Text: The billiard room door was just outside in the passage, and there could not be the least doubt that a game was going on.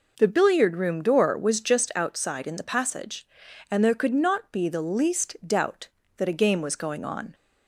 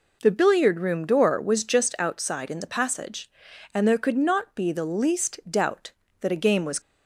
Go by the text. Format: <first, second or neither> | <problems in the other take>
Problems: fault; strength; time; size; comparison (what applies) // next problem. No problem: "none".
first | stops before "going on"; at 6.7 s